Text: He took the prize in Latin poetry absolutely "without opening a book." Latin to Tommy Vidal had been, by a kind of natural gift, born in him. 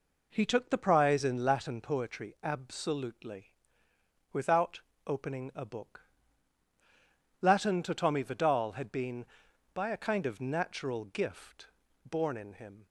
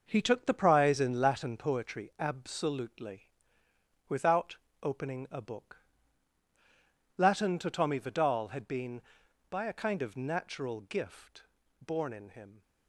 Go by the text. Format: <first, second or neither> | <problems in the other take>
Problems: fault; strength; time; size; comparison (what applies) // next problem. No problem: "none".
first | gets quieter; strong; throughout; 7.5 dB // pauses between "absolutely" and "without"; noticeable; at 3.2 s; 0.80 s long; noticeable in the first // pauses between "without" and "opening"; slight; at 4.5 s; 0.26 s long; slight in the first